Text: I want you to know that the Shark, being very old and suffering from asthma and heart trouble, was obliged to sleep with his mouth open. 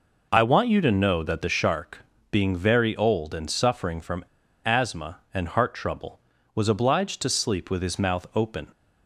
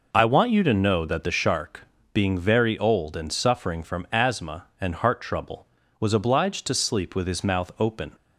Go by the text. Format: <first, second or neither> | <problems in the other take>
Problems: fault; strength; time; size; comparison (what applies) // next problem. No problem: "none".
second | pauses between "from" and "asthma"; at 4.2 s; 0.37 s long